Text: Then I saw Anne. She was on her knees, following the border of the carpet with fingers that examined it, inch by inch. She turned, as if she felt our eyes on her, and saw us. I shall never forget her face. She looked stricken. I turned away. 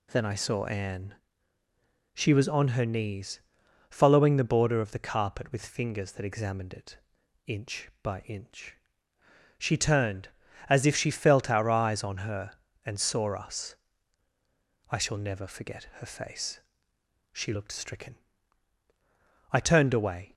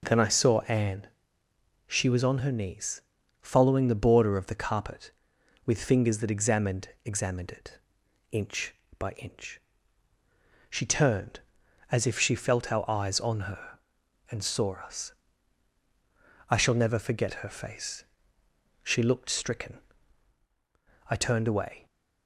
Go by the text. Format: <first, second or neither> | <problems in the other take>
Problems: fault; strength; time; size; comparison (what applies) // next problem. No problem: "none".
first | says "examined" twice; at 7.0 s